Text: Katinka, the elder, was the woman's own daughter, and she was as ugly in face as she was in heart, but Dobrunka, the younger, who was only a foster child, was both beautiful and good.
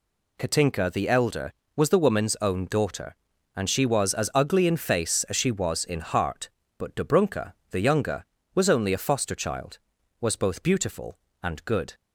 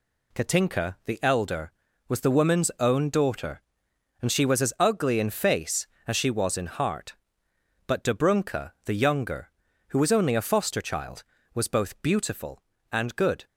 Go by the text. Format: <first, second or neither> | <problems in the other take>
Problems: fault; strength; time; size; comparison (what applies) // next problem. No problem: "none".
second | skips "who"; at 8.4 s